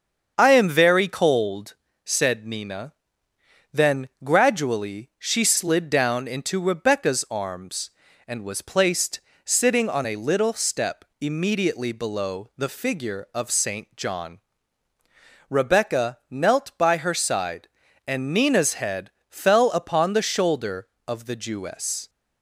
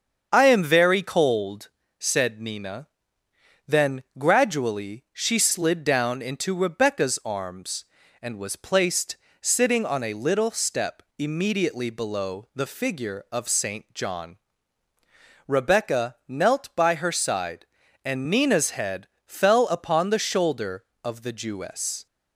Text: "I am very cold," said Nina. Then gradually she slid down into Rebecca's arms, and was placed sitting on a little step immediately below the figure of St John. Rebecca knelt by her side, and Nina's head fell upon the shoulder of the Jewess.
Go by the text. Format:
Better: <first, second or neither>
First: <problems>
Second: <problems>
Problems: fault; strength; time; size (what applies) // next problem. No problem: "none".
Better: neither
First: starts louder than the rest; until 1.3 s; 7 dB // pauses between "placed" and "sitting"; slight; at 9.1 s; 0.26 s long // pauses between "head" and "fell"; slight; at 19.1 s; 0.18 s long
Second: starts louder than the rest; until 1.3 s; 7 dB // pauses between "placed" and "sitting"; slight; at 9.1 s; 0.26 s long // pauses between "head" and "fell"; slight; at 19.0 s; 0.18 s long